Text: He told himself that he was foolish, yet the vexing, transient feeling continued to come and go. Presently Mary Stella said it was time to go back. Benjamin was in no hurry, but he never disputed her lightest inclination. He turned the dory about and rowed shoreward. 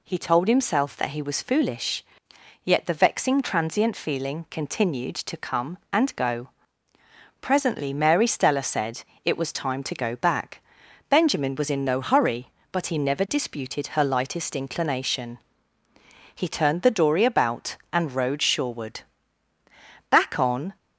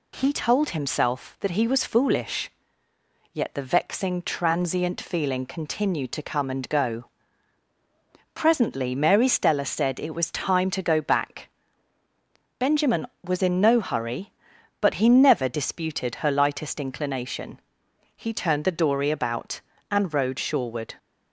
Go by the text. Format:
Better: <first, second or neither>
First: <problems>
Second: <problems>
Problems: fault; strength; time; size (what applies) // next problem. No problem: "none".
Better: second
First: pauses between "said" and "it"; slight; at 9.0 s; 0.20 s long // goes on to say "Back on"; noticeable; from 20.0 s on; 0.66 s long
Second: none